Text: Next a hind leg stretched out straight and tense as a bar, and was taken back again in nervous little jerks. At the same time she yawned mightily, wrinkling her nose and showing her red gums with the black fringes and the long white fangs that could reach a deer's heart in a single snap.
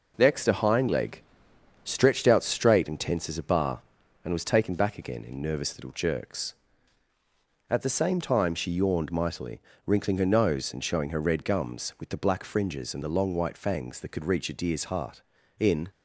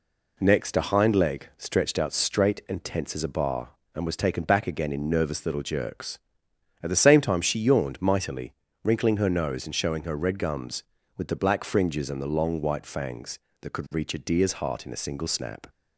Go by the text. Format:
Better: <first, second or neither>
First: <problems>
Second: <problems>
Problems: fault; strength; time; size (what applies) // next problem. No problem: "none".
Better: second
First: pauses between "leg" and "stretched"; noticeable; at 1.2 s; 0.60 s long // stops before "a single snap"; at 15.9 s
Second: none